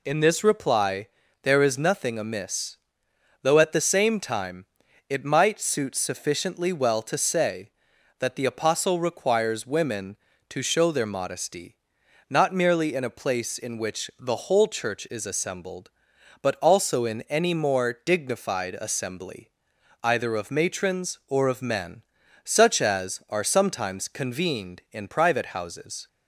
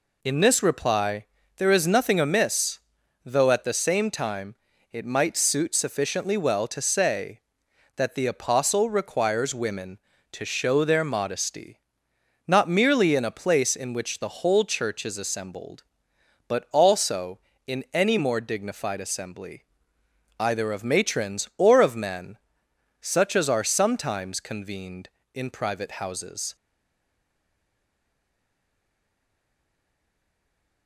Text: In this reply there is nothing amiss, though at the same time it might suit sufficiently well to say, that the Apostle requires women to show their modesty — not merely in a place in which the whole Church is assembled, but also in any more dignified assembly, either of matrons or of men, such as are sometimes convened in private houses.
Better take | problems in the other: first | pauses between "reply" and "there"; slight; at 1.2 s; 0.32 s long; slight in the first // pauses between "time" and "it"; at 4.5 s; 0.38 s long; also in the first // stays silent after the last word; strong; from 26.5 s on; 4.3 s long

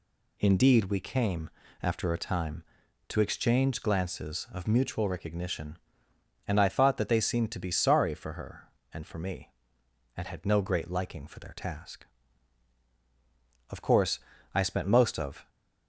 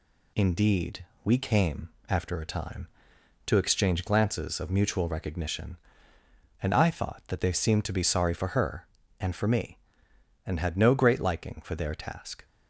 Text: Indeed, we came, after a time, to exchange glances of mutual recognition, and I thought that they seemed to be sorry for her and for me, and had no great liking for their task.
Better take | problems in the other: second | goes on to say "Of course I spent most of"; strong; from 13.6 s on; 1.8 s long

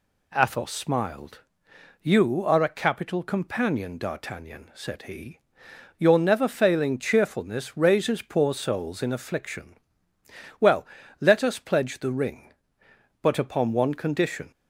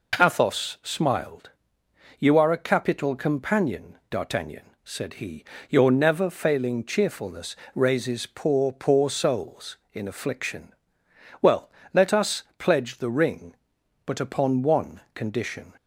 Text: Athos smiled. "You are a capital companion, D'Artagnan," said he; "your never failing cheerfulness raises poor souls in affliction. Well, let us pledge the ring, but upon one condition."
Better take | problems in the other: first | pauses between "cheerfulness" and "raises"; slight; at 7.5 s; 0.18 s long // says "poor" twice; at 8.6 s // pauses between "us" and "pledge"; slight; at 12.4 s; 0.16 s long // pauses between "one" and "condition"; slight; at 14.9 s; 0.16 s long

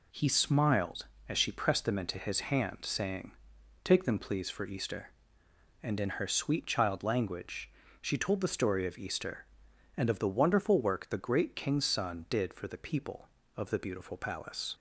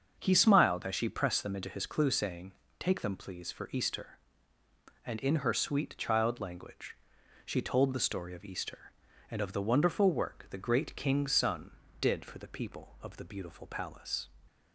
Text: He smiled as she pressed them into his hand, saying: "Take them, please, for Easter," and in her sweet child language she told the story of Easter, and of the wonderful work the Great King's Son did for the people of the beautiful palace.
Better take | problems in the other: first | starts louder than the rest; until 1.1 s; 6.5 dB // says "clue" for "hand"; at 1.8 s // pauses between "language" and "she"; noticeable; at 6.9 s; 0.48 s long; slight in the first

